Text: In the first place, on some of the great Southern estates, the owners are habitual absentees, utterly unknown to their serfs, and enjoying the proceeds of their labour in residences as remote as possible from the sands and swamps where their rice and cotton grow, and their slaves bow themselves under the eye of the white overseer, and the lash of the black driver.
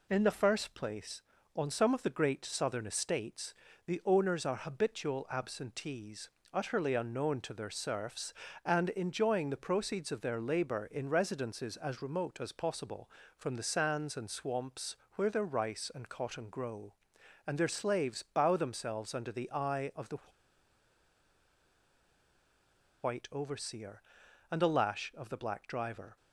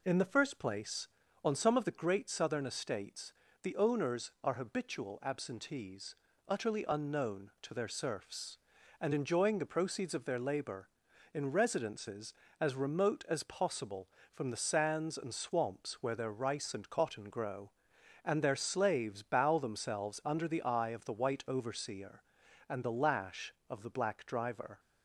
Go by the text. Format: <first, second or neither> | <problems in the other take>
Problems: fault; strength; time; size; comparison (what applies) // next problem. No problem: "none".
second | pauses between "swamps" and "where"; slight; at 14.9 s; 0.20 s long // pauses between "the" and "white"; strong; at 20.1 s; 2.8 s long